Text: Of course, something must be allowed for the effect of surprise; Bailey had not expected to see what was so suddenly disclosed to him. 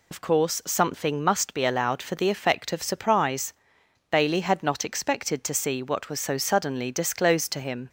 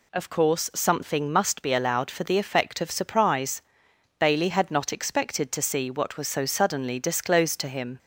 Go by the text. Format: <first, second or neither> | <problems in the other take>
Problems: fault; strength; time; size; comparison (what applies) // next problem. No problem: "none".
second | loses the start of "Of"; at 0.1 s; 85 ms